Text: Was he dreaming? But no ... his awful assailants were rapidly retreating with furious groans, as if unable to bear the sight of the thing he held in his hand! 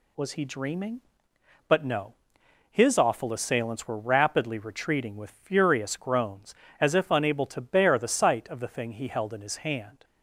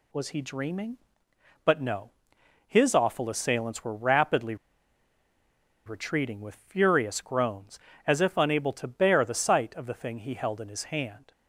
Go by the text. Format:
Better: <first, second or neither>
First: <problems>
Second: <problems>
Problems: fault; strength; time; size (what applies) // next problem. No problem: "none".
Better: first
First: none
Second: pauses between "rapidly" and "retreating"; strong; at 4.5 s; 1.3 s long